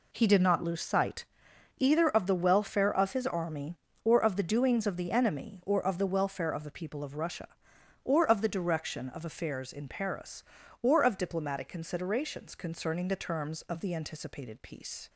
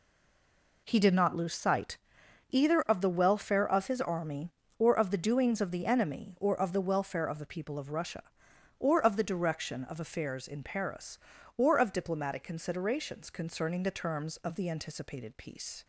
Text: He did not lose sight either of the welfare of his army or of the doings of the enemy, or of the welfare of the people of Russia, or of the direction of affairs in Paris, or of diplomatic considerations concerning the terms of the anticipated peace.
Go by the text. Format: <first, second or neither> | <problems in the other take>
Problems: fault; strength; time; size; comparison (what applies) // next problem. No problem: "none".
first | stays silent before the first word; slight; until 0.8 s; 0.8 s long // pauses between "sight" and "either"; noticeable; at 1.9 s; 0.54 s long; noticeable in the first